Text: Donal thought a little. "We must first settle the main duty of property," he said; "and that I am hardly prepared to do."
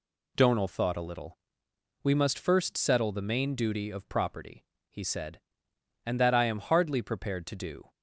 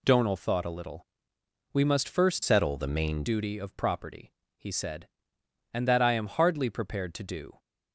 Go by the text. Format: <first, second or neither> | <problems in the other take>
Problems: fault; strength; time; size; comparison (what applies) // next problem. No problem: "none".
first | changes voice from "settle" to "main"; from 2.4 to 3.2 s; 0.8 s long